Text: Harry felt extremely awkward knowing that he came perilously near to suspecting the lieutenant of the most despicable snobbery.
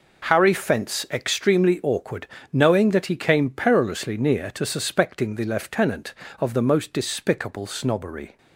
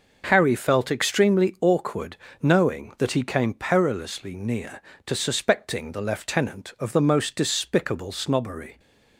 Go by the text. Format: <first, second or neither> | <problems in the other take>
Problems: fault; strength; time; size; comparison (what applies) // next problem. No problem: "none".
second | says "fence" for "felt"; at 0.5 s // pauses between "awkward" and "knowing"; slight; at 2.2 s; 0.26 s long; slight in the second